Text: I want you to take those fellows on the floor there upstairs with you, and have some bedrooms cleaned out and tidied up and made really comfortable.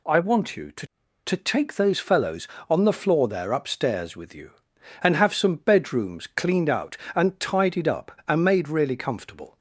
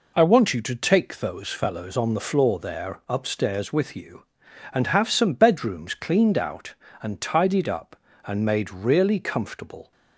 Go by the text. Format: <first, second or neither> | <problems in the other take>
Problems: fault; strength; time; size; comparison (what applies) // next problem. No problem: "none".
second | says "to" twice; at 1.2 s